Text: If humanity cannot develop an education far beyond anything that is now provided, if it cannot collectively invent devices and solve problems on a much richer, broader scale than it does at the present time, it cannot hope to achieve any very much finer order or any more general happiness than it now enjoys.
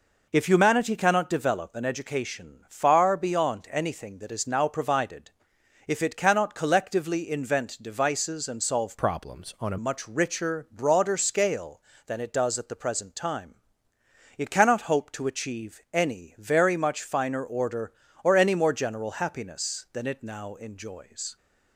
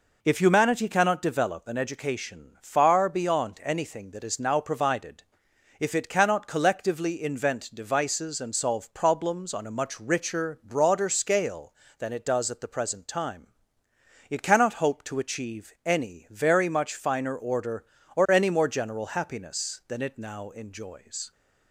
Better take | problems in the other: second | changes voice from "problems" to "a"; from 8.9 to 9.7 s; 0.8 s long

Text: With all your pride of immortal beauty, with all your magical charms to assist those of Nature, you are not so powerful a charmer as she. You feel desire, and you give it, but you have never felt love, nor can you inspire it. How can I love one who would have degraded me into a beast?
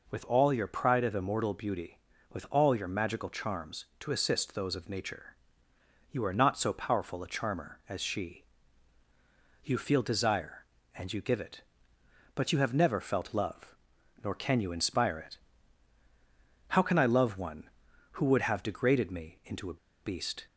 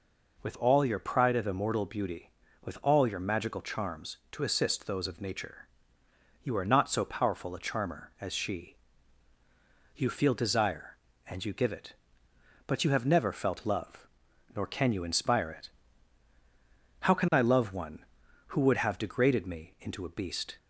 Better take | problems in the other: second | pauses between "a" and "beast"; slight; at 19.7 s; 0.26 s long

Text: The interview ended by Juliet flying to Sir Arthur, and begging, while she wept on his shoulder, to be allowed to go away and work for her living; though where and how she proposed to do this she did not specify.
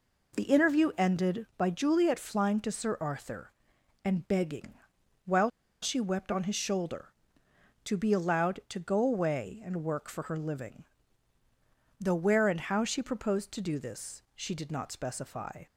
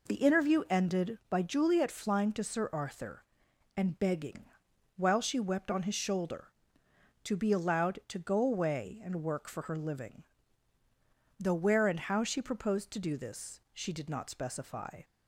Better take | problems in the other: second | pauses between "while" and "she"; slight; at 5.4 s; 0.33 s long

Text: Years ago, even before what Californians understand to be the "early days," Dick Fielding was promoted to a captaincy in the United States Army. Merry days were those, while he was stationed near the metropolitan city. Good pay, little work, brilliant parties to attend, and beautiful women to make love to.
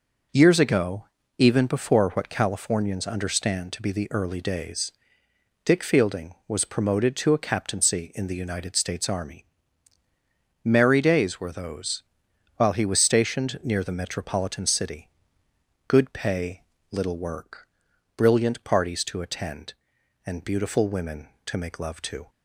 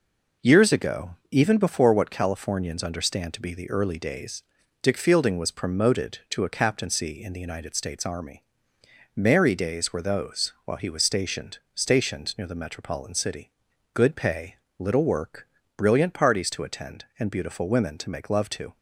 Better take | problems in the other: first | says "stationed" twice; at 11.7 s

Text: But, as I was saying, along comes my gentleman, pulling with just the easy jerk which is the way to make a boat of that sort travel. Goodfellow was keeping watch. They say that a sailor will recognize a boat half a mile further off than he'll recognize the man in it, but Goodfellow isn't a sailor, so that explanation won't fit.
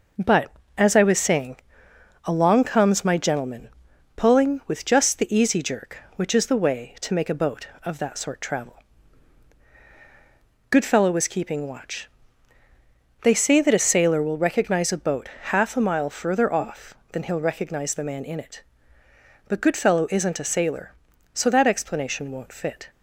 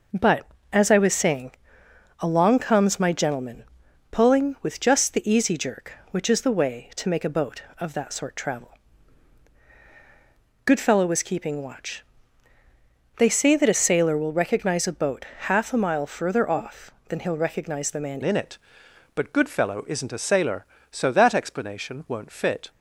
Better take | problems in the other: first | pauses between "boat" and "half"; slight; at 15.2 s; 0.16 s long; slight in the first // changes voice at "in"; from 18.2 s on; 4.4 s long

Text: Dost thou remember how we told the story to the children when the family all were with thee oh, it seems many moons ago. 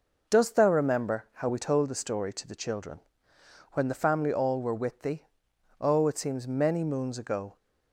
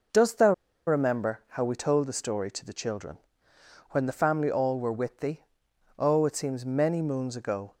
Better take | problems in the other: first | pauses between "thou" and "remember"; slight; at 0.5 s; 0.35 s long // pauses between "children" and "when"; noticeable; at 3.1 s; 0.72 s long; noticeable in the first // pauses between "thee" and "oh"; noticeable; at 5.4 s; 0.54 s long; noticeable in the first

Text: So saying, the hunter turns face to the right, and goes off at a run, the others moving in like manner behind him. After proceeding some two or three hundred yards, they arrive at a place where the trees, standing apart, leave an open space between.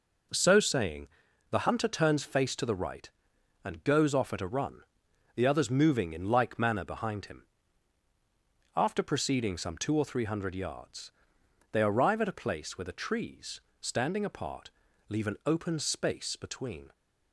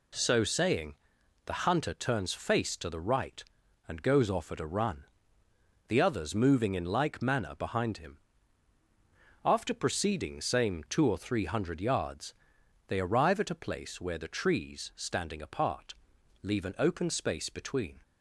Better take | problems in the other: first | says "same" for "some"; at 10.3 s

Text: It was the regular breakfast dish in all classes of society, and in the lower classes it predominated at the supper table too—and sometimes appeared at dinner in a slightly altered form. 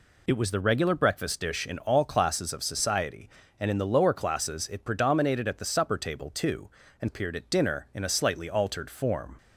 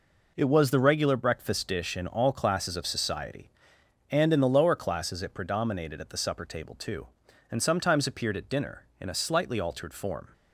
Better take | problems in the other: second | skips "sometimes"; at 7.0 s

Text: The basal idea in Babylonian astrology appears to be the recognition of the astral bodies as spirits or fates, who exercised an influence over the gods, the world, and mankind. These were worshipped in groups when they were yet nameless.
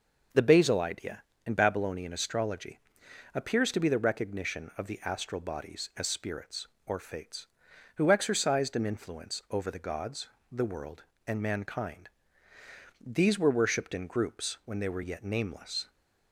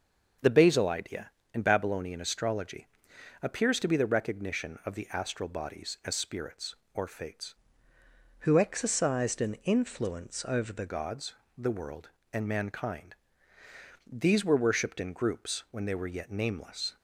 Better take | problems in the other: first | starts louder than the rest; until 1.6 s; 6.5 dB // pauses between "astrology" and "appears"; noticeable; at 2.8 s; 0.56 s long; noticeable in the first // changes voice from "who" to "the"; from 8.3 to 10.8 s; 2.5 s long

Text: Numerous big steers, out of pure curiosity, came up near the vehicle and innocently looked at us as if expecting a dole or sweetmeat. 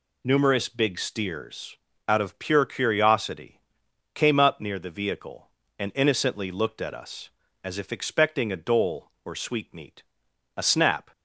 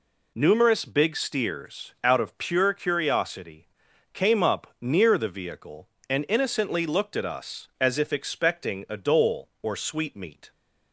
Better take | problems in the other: second | goes on to say "A snap"; from 10.5 s on; 0.54 s long

